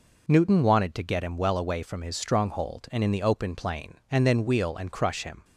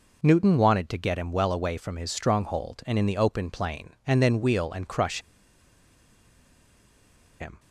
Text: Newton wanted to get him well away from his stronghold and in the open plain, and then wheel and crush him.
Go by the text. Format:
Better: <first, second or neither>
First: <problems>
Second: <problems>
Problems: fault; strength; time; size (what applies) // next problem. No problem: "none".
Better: first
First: none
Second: pauses between "crush" and "him"; strong; at 5.1 s; 2.2 s long